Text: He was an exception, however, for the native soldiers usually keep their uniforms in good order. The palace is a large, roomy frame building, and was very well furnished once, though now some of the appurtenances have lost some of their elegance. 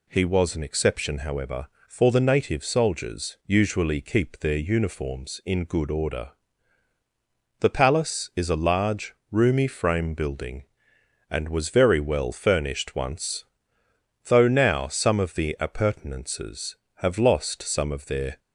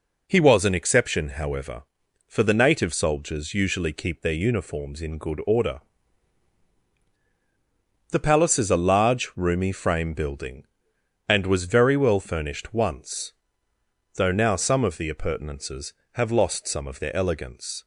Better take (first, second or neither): second